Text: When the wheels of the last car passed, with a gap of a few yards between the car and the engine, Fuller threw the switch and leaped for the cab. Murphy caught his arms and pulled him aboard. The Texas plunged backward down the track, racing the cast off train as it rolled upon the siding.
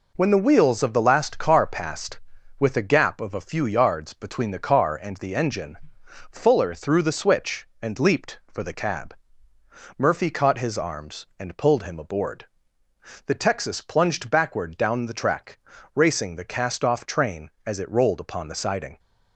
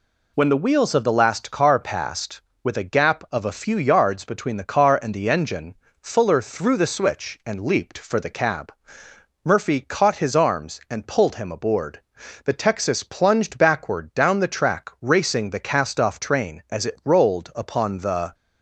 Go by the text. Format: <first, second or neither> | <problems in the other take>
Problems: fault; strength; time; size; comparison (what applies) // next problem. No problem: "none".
first | stops before "siding"; at 18.3 s